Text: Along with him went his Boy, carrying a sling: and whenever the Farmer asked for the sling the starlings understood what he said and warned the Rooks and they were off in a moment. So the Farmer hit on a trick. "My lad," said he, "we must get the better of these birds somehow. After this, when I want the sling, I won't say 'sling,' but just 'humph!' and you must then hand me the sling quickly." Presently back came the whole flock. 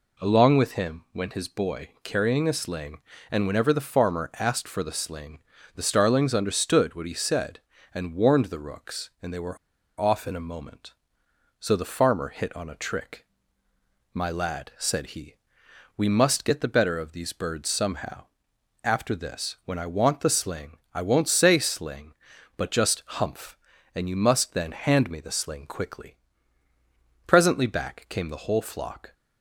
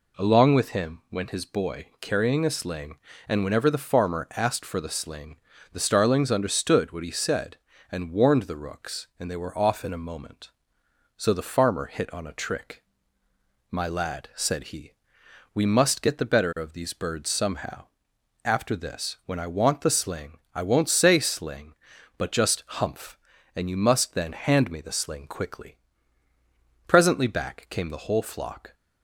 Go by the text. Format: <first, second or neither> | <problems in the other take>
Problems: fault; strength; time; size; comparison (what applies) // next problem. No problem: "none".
second | pauses between "sling" and "the"; slight; at 5.3 s; 0.36 s long; slight in the second // pauses between "were" and "off"; at 9.5 s; 0.43 s long